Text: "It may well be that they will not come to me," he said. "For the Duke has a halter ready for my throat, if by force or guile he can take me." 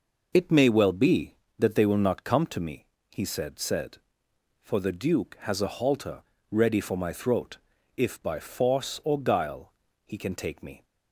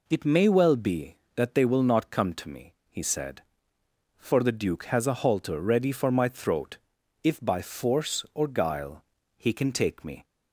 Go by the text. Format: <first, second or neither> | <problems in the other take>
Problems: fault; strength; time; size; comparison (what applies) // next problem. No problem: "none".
second | says "said" twice; at 3.5 s // pauses between "halter" and "ready"; slight; at 6.2 s; 0.28 s long // pauses between "guile" and "he"; slight; at 9.7 s; 0.34 s long; slight in the second